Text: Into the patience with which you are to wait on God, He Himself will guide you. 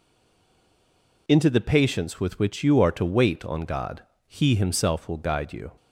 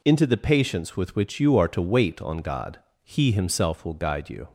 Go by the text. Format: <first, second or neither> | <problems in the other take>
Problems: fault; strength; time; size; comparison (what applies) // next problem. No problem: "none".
second | stays silent before the first word; noticeable; until 1.2 s; 1.2 s long